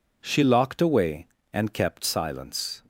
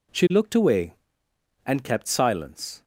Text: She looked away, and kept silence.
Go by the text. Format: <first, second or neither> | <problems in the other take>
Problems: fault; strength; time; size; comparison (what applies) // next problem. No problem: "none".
second | says "locked" for "looked"; at 0.4 s